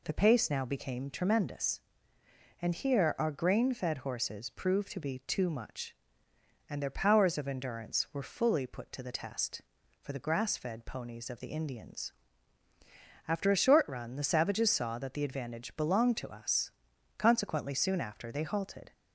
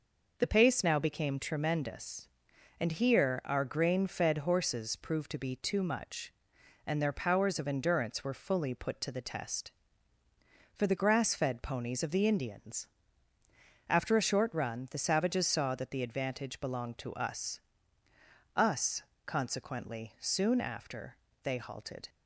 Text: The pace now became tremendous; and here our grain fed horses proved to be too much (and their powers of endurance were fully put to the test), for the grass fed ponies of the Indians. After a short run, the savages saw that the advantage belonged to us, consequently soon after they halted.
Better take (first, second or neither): first